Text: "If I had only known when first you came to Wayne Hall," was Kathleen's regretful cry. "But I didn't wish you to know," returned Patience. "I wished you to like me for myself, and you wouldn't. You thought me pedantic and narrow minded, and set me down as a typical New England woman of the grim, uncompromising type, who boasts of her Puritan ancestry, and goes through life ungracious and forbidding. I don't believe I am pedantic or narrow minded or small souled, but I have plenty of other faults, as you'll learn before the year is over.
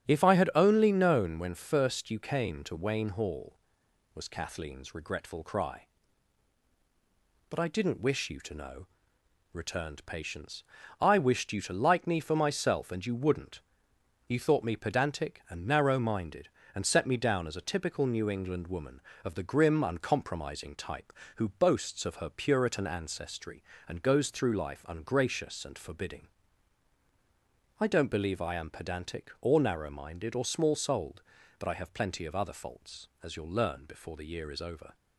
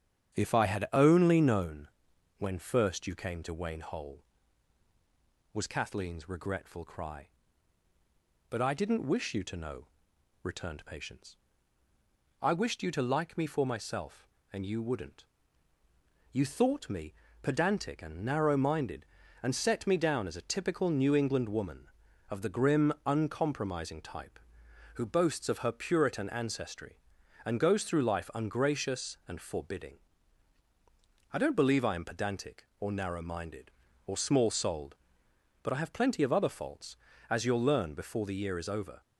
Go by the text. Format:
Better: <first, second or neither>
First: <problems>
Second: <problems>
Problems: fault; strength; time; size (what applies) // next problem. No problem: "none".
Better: first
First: starts louder than the rest; strong; until 1.1 s; 9 dB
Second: starts louder than the rest; strong; until 1.4 s; 9 dB // pauses between "known" and "when"; noticeable; at 1.8 s; 0.50 s long // says "Hole" for "Hall"; at 3.8 s // pauses between "me" and "pedantic"; slight; at 17.1 s; 0.30 s long